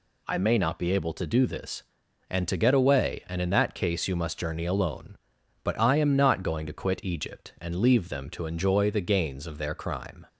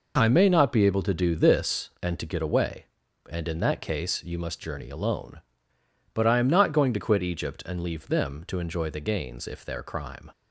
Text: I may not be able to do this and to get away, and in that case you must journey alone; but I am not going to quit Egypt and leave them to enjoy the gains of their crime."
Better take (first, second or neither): first